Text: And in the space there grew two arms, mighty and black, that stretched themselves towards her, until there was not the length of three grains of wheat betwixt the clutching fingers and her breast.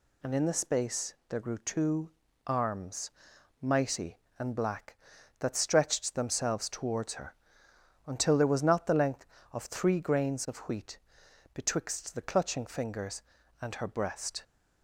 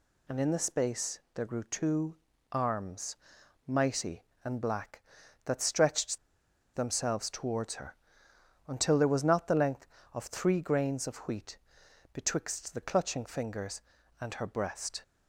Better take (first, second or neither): first